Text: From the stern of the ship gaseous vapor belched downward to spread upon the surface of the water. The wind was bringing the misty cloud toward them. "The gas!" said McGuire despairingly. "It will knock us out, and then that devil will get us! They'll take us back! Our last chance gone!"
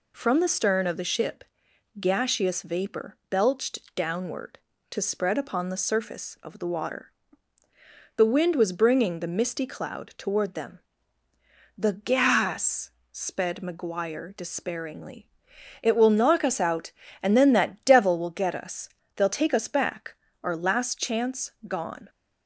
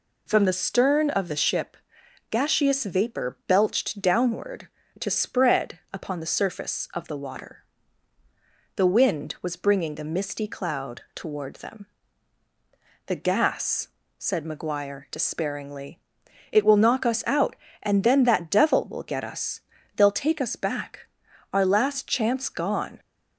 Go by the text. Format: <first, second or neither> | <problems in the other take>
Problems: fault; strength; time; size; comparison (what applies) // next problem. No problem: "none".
second | pauses between "ship" and "gaseous"; noticeable; at 1.4 s; 0.56 s long; noticeable in the second // says "sped" for "said"; at 13.1 s // pauses between "chance" and "gone"; slight; at 21.5 s; 0.16 s long